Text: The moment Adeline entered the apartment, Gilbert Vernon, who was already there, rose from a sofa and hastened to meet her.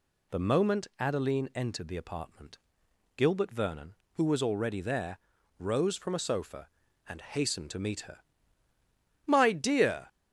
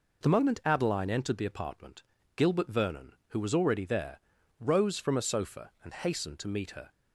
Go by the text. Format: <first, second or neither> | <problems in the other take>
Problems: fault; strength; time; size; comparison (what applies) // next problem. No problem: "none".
second | goes on to say "My dear"; noticeable; from 9.2 s on; 0.84 s long